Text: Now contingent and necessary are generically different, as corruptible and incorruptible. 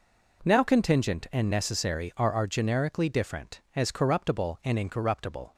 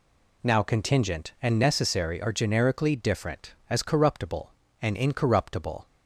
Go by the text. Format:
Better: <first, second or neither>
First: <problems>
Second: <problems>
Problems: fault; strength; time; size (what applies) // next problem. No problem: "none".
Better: second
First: says "are" twice; at 2.3 s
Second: none